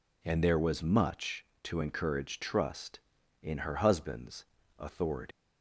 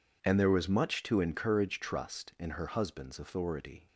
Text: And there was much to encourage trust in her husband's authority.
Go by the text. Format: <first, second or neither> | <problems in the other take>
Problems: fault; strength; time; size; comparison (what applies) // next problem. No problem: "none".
second | pauses between "husband's" and "authority"; slight; at 4.4 s; 0.34 s long // leaves "authority" unfinished; at 5.3 s; 155 ms